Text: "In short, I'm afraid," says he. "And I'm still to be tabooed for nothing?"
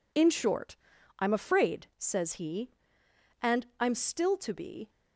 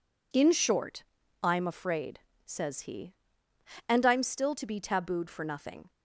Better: second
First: stops before "tabooed for nothing"; at 4.8 s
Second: none

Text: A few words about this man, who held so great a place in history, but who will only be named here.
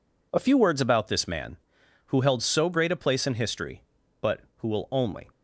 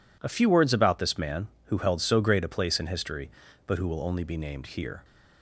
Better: second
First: stops before "be named here"; at 5.3 s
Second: none

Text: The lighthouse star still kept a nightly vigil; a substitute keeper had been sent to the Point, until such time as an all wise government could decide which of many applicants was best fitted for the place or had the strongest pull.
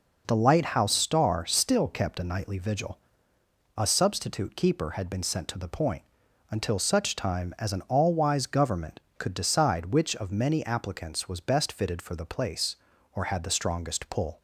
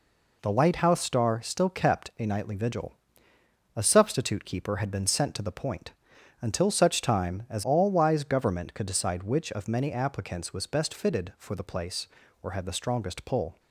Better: first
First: none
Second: skips "an"; at 7.6 s

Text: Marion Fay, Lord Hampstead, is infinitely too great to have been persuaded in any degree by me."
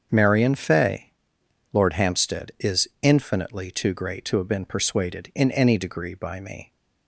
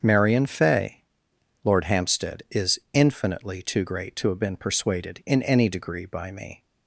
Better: neither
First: starts louder than the rest; until 1.1 s; 7 dB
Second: starts louder than the rest; until 1.0 s; 7 dB

